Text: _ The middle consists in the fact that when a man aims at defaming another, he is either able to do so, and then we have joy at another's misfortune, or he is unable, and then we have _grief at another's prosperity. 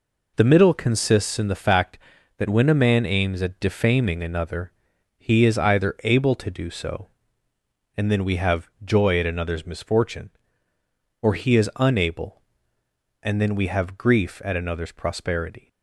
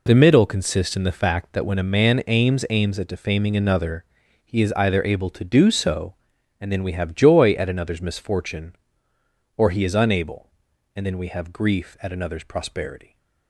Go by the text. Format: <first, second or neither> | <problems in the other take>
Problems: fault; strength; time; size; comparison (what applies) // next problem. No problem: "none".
first | says "aims" twice; at 2.6 s